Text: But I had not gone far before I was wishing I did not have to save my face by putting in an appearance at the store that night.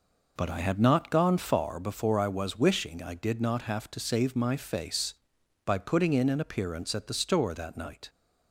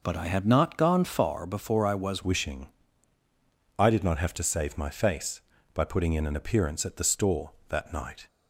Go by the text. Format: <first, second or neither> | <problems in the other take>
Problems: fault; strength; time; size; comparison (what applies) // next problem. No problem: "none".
first | changes voice at "wishing"; from 2.2 s on; 6.0 s long // pauses between "wishing" and "I"; at 2.6 s; 1.1 s long